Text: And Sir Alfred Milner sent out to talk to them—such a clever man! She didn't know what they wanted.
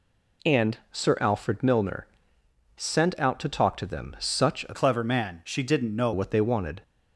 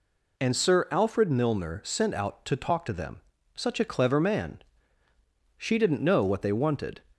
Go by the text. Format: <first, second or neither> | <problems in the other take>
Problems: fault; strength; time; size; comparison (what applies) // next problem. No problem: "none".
second | pauses between "Milner" and "sent"; noticeable; at 2.0 s; 0.70 s long // changes voice from "clever" to "know"; from 4.7 to 6.1 s; 1.4 s long